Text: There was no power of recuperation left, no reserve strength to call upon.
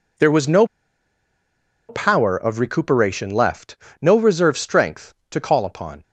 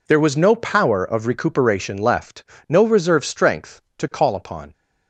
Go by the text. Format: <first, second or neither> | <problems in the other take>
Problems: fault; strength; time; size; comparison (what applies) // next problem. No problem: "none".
second | pauses between "no" and "power"; at 0.6 s; 1.2 s long